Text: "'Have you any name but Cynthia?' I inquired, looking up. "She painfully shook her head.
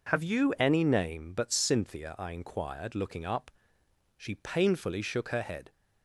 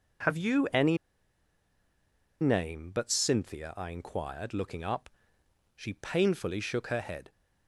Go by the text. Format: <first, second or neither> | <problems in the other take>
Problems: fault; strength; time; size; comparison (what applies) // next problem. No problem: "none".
first | pauses between "any" and "name"; strong; at 0.9 s; 1.4 s long